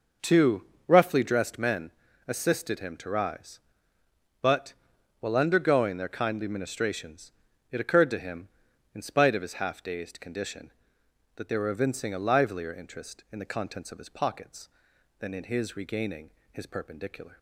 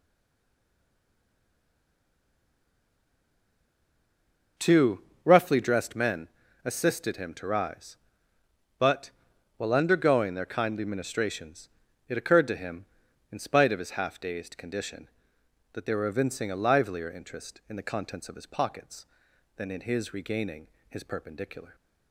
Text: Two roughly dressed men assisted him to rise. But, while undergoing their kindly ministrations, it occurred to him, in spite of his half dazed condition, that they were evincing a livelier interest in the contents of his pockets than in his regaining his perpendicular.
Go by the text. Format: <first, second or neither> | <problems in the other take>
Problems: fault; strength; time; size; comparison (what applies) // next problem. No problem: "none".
first | stays silent before the first word; strong; until 4.5 s; 4.5 s long // pauses between "Two" and "roughly"; slight; at 5.0 s; 0.24 s long; slight in the first // pauses between "men" and "assisted"; slight; at 6.2 s; 0.34 s long; slight in the first // pauses between "regaining" and "his"; slight; at 20.6 s; 0.22 s long; slight in the first